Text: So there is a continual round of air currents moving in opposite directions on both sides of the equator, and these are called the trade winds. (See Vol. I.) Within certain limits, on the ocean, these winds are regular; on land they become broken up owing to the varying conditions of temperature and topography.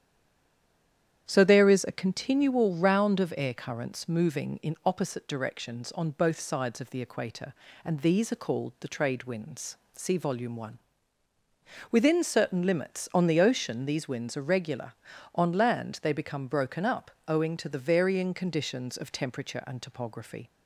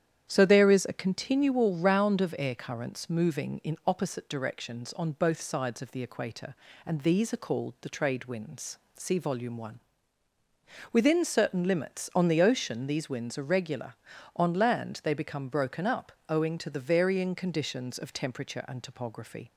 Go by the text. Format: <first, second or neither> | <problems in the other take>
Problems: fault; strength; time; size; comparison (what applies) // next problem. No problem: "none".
second | stays silent before the first word; noticeable; until 1.2 s; 1.2 s long // starts louder than the rest; strong; until 2.2 s; 9.5 dB; strong in the second // pauses between "up" and "owing"; slight; at 17.1 s; 0.16 s long; slight in the second